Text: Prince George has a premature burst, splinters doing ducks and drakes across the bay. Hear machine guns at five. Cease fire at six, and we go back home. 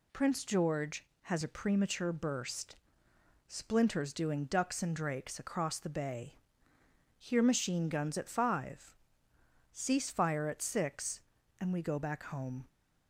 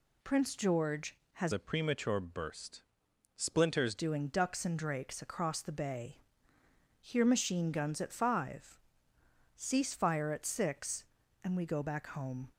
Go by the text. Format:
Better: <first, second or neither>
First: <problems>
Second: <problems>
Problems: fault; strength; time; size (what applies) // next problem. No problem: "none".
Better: first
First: none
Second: changes voice from "a" to "splinters"; from 1.5 to 3.9 s; 2.4 s long